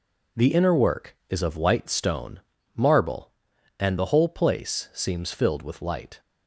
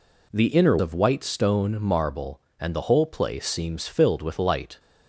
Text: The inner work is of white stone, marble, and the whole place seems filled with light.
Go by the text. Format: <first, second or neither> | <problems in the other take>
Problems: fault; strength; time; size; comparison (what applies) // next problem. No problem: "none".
first | skips "work is"; at 0.7 s